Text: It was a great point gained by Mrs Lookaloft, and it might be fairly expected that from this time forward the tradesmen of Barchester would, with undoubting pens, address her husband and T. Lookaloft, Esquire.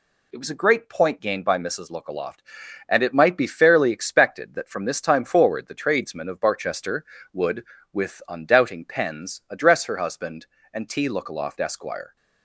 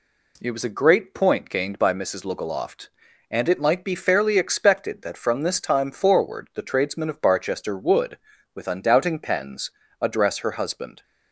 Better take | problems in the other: first | stops before "and T Lookaloft Esquire"; at 11.0 s

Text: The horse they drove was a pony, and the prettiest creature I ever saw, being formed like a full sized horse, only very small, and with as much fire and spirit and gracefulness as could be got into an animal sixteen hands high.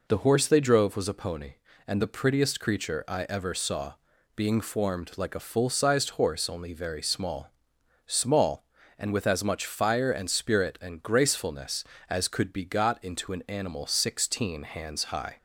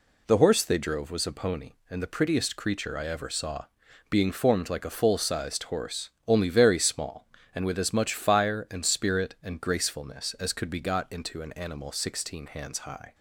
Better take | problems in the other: second | says "small" twice; at 8.0 s

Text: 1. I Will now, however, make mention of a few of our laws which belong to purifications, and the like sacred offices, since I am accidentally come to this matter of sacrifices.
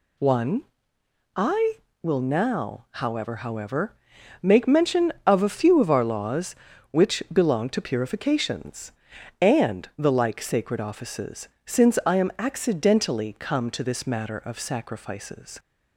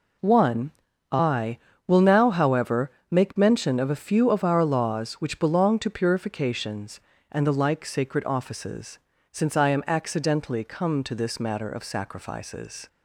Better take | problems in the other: second | says "however" twice; at 3.3 s

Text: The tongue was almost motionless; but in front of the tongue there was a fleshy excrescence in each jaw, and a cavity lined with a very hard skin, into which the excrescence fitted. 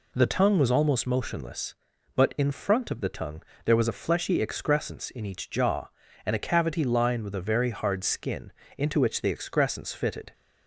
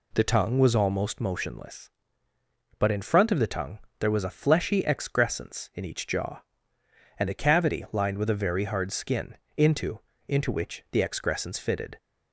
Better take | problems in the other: first | pauses between "tongue" and "there"; slight; at 3.7 s; 0.22 s long; slight in the first // says "into" twice; at 10.2 s

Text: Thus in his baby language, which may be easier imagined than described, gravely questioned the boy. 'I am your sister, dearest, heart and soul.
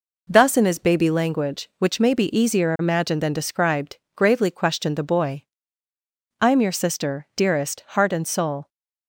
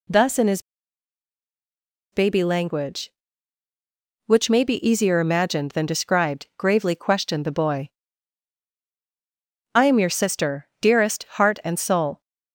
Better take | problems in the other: first | pauses between "his" and "baby"; strong; at 0.6 s; 1.5 s long

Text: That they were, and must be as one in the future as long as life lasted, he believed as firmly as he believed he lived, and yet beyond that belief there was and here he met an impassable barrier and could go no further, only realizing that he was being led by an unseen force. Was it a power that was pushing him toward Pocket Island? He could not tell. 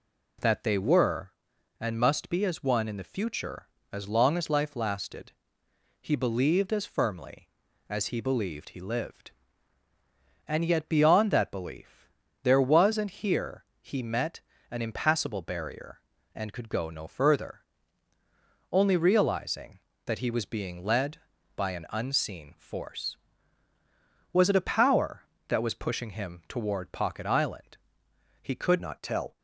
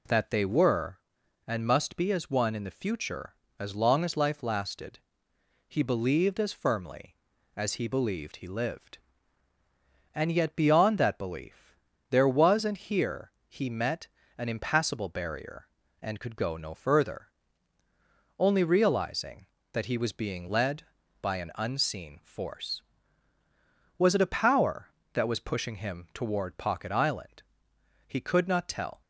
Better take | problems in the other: second | pauses between "belief" and "there"; slight; at 12.0 s; 0.34 s long; slight in the second // pauses between "here" and "he"; slight; at 13.6 s; 0.16 s long; slight in the second // pauses between "met" and "an"; slight; at 14.3 s; 0.32 s long; slight in the second // changes voice at "not"; from 28.8 s on; 0.5 s long

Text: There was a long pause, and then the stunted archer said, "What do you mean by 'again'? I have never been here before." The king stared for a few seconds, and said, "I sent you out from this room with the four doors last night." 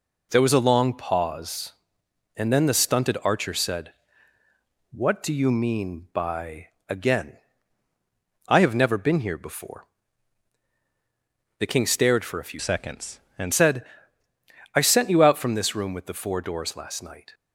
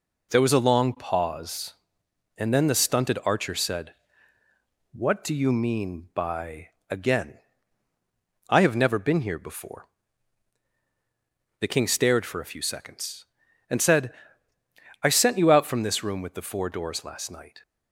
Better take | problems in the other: second | pauses between "by" and "again"; slight; at 6.6 s; 0.20 s long; slight in the second // changes voice from "seconds" to "and"; from 12.5 to 13.5 s; 1.0 s long

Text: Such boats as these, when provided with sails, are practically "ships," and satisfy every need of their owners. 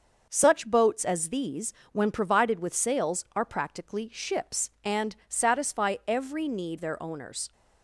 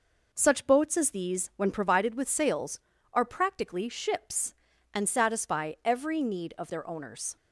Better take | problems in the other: second | starts louder than the rest; until 1.3 s; 6.5 dB // skips "of"; at 6.7 s

